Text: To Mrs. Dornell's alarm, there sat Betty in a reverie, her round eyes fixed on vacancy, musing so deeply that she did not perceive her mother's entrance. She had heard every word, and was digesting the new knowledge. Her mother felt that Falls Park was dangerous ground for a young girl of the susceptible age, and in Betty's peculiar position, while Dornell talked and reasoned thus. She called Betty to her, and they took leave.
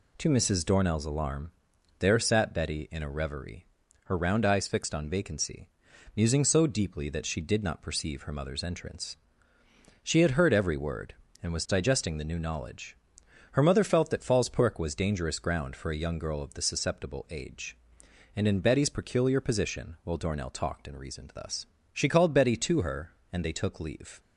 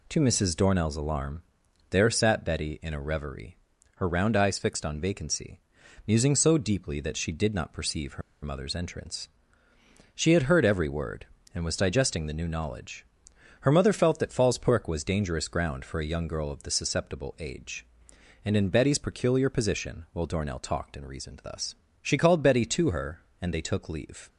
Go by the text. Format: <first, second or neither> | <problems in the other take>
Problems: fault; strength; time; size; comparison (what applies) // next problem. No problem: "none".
first | pauses between "her" and "mother's"; slight; at 8.2 s; 0.21 s long